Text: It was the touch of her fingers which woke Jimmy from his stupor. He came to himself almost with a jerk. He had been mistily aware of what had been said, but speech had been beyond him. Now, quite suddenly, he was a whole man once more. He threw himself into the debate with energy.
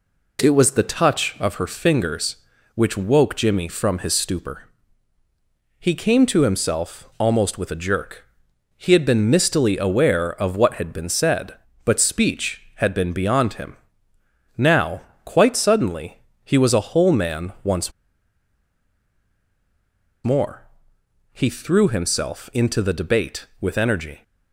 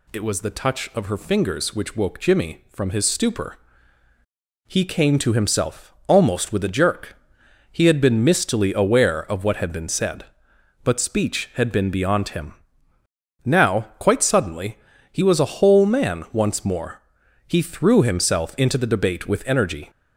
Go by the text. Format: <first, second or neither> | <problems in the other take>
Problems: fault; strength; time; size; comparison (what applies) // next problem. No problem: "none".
second | pauses between "once" and "more"; strong; at 17.9 s; 2.3 s long